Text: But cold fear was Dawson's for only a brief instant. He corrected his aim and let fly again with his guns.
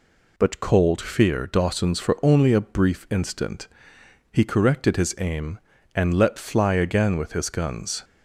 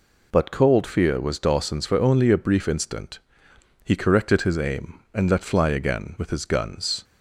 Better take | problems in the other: second | skips "was"; at 1.4 s

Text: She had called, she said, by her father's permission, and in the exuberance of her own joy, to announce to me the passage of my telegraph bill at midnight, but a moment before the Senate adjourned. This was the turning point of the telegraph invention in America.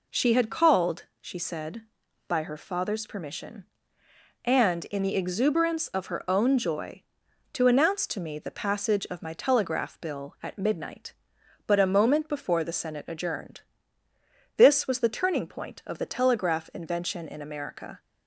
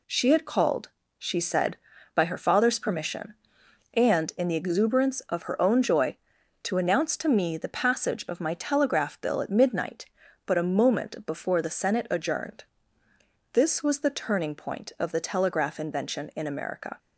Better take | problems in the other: neither | none

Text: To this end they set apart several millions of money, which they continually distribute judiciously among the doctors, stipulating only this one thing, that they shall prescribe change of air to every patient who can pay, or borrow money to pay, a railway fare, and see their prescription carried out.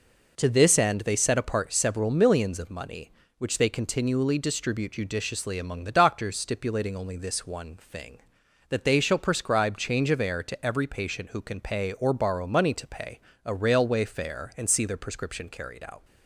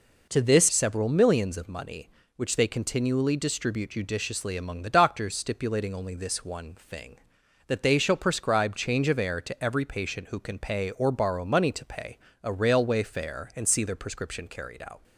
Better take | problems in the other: first | skips "end they set apart"; at 0.7 s

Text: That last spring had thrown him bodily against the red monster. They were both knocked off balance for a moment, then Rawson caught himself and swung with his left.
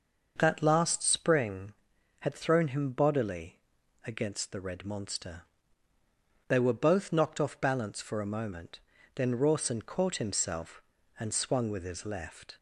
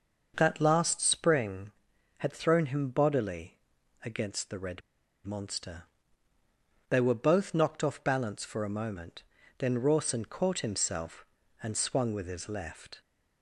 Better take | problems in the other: first | starts louder than the rest; noticeable; until 1.3 s; 6 dB; noticeable in the first // pauses between "bodily" and "against"; noticeable; at 3.5 s; 0.46 s long; noticeable in the first // pauses between "red" and "monster"; at 4.8 s; 0.45 s long

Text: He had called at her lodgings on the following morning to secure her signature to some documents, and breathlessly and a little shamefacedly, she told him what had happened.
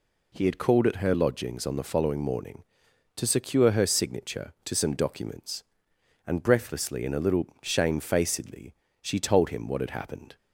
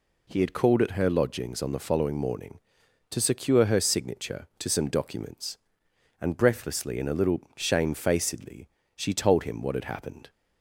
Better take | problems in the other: neither | none

